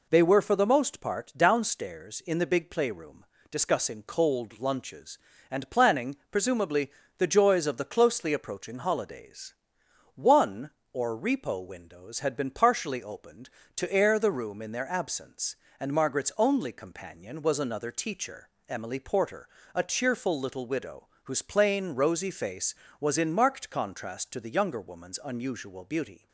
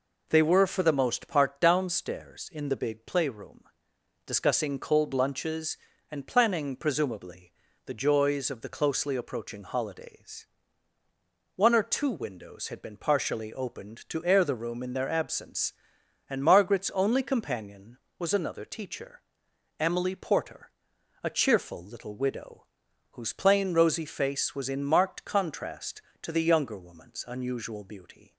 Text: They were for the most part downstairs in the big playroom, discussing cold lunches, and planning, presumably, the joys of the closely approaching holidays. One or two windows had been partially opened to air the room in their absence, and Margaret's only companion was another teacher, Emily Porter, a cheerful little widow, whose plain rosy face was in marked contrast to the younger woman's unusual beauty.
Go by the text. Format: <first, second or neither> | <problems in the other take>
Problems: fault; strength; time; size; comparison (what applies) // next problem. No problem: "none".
second | says "repo" for "two"; at 11.1 s